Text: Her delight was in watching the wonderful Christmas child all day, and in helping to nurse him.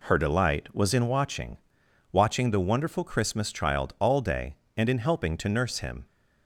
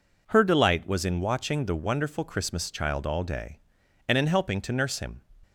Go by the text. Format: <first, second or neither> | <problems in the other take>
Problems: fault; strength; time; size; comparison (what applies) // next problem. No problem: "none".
second | says "watching" twice; at 2.0 s